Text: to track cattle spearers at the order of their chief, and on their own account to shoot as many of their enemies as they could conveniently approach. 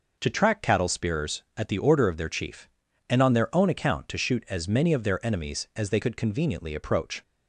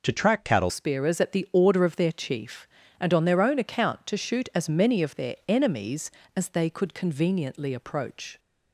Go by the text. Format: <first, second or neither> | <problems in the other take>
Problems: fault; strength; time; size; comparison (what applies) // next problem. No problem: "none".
first | changes voice at "spearers"; from 0.6 s on; 7.7 s long